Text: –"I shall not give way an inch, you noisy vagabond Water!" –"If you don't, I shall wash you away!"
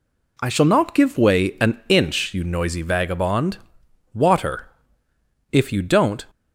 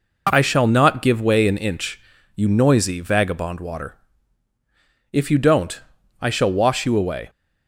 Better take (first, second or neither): second